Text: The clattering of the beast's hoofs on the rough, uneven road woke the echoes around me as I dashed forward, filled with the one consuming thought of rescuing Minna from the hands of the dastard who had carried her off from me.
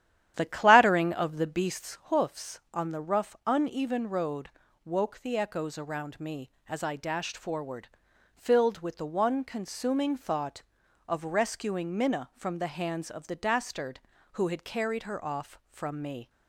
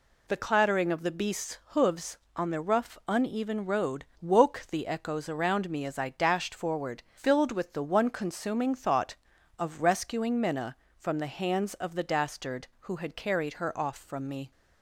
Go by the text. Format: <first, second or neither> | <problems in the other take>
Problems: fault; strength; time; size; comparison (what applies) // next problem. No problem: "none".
second | starts louder than the rest; strong; until 2.1 s; 11.5 dB // pauses between "road" and "woke"; slight; at 4.4 s; 0.34 s long; slight in the second